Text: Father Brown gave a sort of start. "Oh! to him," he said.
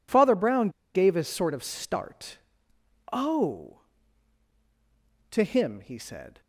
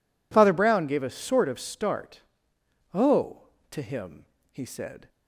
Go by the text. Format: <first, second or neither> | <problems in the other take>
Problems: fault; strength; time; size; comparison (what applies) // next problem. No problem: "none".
second | pauses between "Brown" and "gave"; slight; at 0.6 s; 0.25 s long